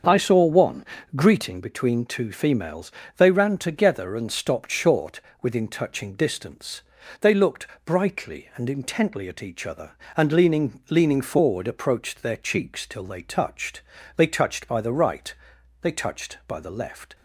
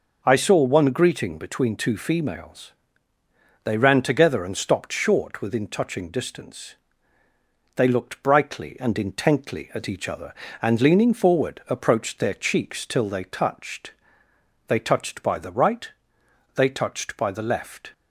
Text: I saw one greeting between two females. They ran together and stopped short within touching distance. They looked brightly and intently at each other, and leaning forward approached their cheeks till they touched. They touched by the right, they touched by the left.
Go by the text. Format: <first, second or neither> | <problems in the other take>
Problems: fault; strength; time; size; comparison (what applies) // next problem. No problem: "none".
second | starts louder than the rest; until 1.3 s; 7 dB // pauses between "one" and "greeting"; slight; at 0.8 s; 0.30 s long // pauses between "short" and "within"; slight; at 5.1 s; 0.22 s long // pauses between "looked" and "brightly"; slight; at 7.6 s; 0.22 s long // says "leaning" twice; at 10.9 s